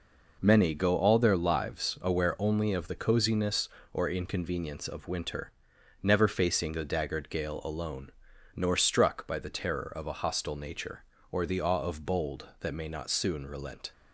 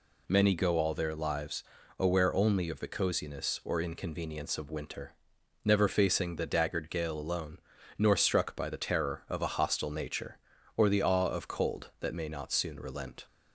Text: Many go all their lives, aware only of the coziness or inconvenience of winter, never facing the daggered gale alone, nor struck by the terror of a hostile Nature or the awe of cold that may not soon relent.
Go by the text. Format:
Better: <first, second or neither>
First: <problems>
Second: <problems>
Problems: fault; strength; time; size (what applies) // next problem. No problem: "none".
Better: second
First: says "bold" for "cold"; at 12.0 s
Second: none